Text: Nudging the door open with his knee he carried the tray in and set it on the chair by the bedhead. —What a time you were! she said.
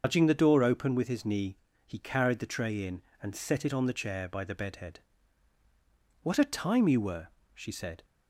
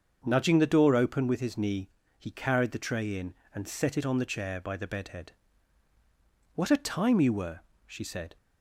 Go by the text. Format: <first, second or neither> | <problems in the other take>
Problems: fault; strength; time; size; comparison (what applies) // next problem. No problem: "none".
second | loses the start of "Nudging"; at 0.0 s; 140 ms // starts louder than the rest; until 1.0 s; 6.5 dB; also in the second // pauses between "knee" and "he"; slight; at 1.5 s; 0.28 s long; slight in the second